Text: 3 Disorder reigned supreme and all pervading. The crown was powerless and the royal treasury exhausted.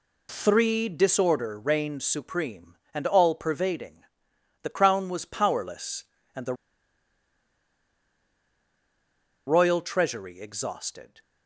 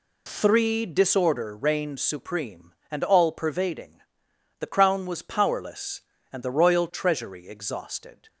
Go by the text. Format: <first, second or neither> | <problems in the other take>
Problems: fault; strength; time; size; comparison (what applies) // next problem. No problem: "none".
second | pauses between "the" and "royal"; strong; at 6.5 s; 2.9 s long